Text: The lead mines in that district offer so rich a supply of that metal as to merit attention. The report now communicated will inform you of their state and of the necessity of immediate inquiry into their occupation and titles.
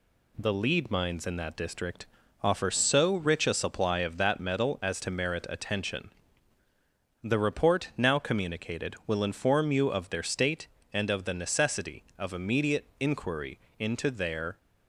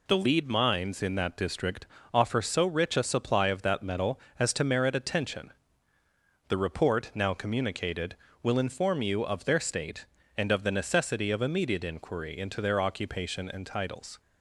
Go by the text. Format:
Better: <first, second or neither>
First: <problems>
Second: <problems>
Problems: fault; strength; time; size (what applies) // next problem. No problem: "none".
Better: second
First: pauses between "district" and "offer"; slight; at 2.0 s; 0.36 s long // pauses between "inquiry" and "into"; slight; at 13.5 s; 0.20 s long // stops before "occupation and titles"; at 14.5 s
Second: pauses between "district" and "offer"; slight; at 1.8 s; 0.26 s long